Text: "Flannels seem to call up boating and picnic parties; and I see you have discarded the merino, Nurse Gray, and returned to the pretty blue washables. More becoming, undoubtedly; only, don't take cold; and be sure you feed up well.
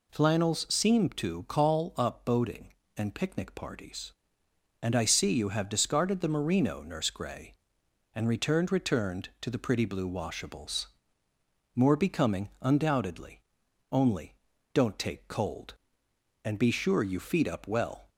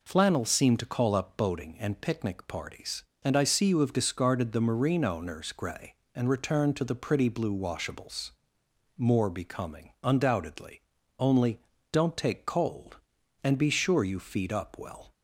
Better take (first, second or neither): second